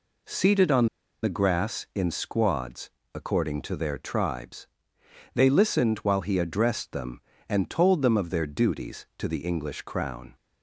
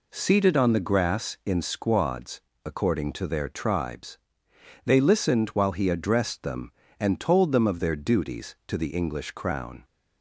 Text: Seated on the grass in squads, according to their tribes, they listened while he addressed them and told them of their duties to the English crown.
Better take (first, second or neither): second